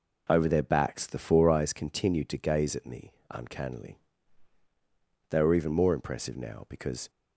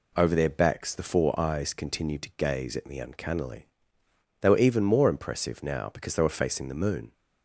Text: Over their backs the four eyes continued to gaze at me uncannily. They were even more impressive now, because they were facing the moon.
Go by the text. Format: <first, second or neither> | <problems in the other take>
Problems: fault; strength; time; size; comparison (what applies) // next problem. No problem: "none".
second | pauses between "me" and "uncannily"; slight; at 3.1 s; 0.16 s long // stops before "they were facing the moon"; at 7.0 s